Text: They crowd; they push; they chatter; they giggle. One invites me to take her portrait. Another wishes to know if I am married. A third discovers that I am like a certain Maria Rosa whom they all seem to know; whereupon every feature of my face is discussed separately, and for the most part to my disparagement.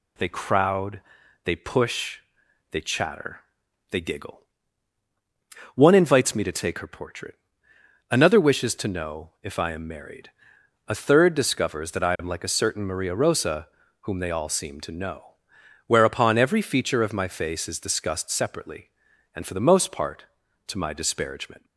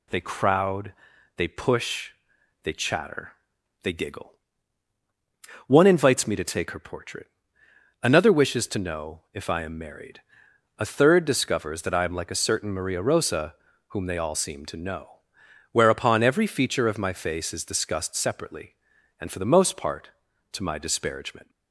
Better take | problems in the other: neither | pauses between "Rosa" and "whom"; slight; the same in both

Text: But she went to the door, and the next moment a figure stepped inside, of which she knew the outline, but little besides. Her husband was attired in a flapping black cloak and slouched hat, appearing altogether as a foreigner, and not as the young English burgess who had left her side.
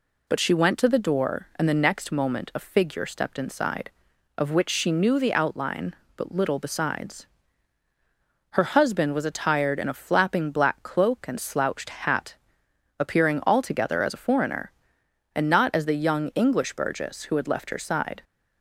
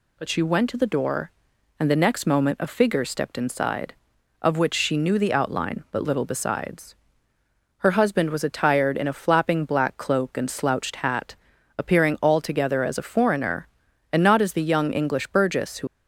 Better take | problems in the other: first | stops before "had left her side"; at 15.8 s

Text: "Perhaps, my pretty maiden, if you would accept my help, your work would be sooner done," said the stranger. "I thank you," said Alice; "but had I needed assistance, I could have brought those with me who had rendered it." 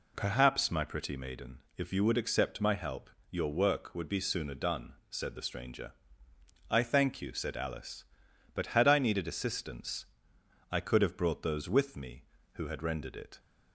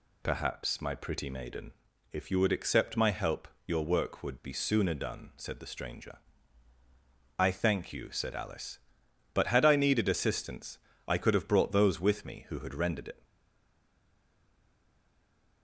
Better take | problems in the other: first | stays silent after the last word; from 13.2 s on; 2.4 s long

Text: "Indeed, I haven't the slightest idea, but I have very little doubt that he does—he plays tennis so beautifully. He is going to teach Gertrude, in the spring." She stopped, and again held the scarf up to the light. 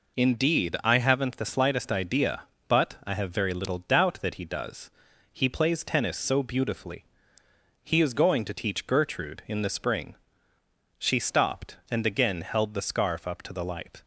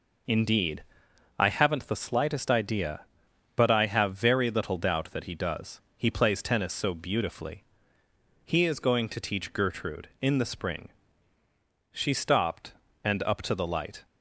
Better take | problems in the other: first | skips "again held the scarf"; at 13.2 s

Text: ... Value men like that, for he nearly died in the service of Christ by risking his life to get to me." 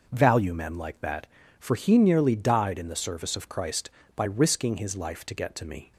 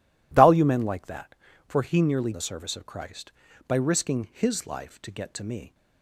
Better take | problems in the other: first | skips "died in"; at 2.3 s

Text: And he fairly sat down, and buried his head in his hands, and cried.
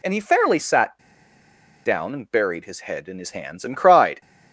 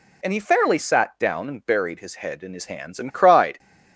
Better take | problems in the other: second | pauses between "sat" and "down"; noticeable; at 0.9 s; 0.86 s long

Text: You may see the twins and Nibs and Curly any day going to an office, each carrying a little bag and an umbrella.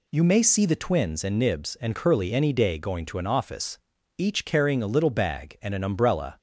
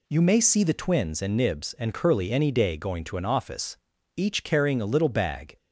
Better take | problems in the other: first | stops before "and an umbrella"; at 5.5 s

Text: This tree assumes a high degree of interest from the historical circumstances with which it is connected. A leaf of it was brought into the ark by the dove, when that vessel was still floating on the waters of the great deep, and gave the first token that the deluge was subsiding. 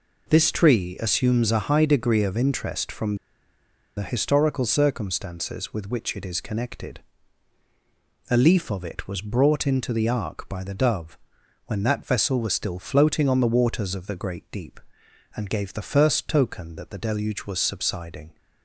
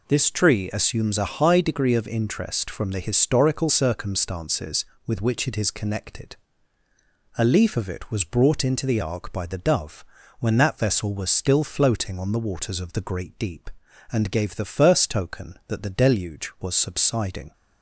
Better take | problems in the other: second | pauses between "from" and "the"; noticeable; at 3.1 s; 0.81 s long

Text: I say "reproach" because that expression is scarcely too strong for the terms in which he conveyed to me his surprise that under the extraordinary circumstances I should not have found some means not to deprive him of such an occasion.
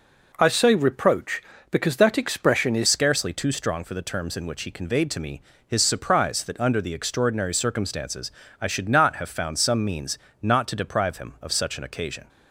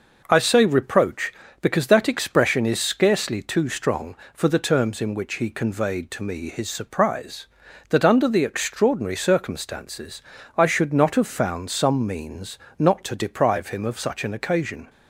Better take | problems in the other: second | changes voice at "scarcely"; from 2.8 s on; 9.4 s long // pauses between "me" and "his"; slight; at 5.4 s; 0.24 s long // pauses between "circumstances" and "I"; slight; at 8.3 s; 0.32 s long; slight in the second // pauses between "means" and "not"; slight; at 10.1 s; 0.24 s long; slight in the second

